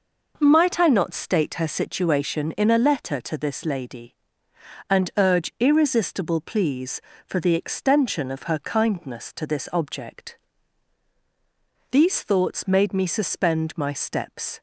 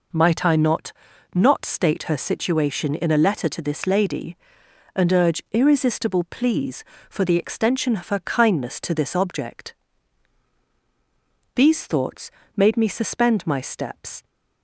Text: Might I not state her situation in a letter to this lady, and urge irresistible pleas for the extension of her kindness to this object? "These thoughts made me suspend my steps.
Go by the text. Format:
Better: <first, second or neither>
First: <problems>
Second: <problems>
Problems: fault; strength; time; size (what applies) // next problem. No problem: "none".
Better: first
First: none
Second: says "not" twice; at 1.3 s // pauses between "thoughts" and "made"; slight; at 12.2 s; 0.28 s long